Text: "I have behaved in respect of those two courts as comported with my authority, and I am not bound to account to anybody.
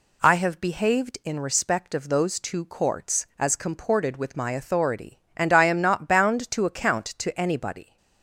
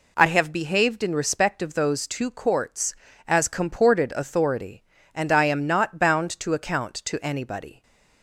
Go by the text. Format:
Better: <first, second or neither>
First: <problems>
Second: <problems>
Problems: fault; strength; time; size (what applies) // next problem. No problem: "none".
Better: first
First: none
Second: skips "with my"; at 4.1 s